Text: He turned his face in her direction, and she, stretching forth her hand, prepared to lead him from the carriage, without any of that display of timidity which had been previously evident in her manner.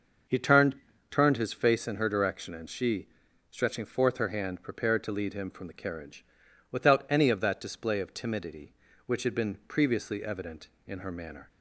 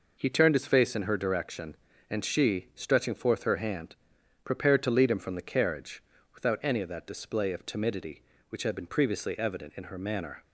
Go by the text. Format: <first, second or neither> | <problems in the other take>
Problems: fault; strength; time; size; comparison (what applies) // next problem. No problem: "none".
second | says "turned" twice; at 1.1 s